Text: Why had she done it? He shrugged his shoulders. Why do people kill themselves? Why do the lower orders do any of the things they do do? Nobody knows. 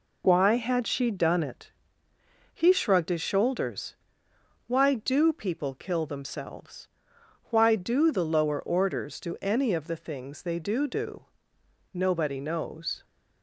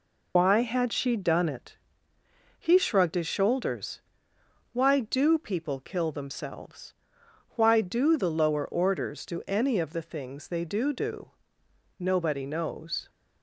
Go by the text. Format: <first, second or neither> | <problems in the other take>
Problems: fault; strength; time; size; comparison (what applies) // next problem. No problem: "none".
first | loses the start of "Why"; at 0.3 s; 50 ms